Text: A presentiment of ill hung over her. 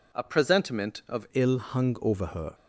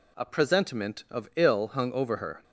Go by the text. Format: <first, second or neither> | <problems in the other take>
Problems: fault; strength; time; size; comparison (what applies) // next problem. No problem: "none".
second | changes voice at "ill"; from 1.3 s on; 1.2 s long